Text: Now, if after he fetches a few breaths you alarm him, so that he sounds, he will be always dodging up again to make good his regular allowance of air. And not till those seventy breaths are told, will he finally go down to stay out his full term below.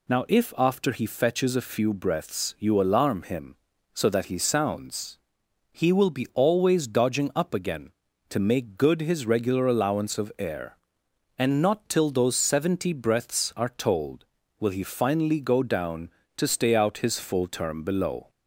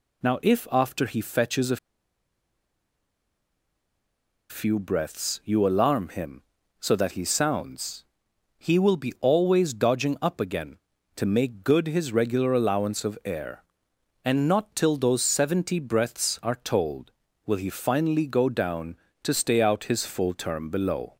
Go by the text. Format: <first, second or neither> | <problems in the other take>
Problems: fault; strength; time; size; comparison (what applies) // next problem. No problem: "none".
first | pauses between "a" and "few"; strong; at 1.7 s; 2.7 s long